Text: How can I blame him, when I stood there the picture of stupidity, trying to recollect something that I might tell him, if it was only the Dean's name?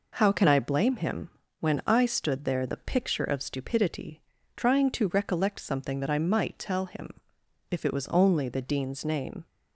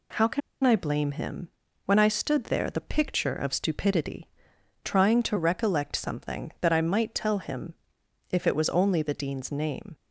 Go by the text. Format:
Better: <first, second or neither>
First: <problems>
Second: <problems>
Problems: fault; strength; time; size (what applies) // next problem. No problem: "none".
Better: first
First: none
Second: pauses between "can" and "I"; slight; at 0.4 s; 0.24 s long